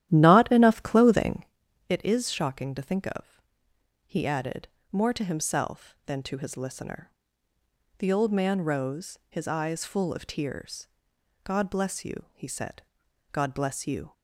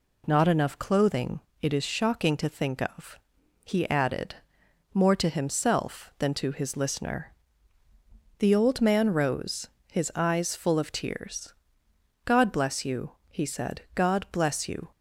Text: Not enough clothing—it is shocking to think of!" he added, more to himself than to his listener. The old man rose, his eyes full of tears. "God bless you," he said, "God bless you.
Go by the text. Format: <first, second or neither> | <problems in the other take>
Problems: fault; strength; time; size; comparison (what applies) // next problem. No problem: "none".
second | starts louder than the rest; strong; until 1.5 s; 12 dB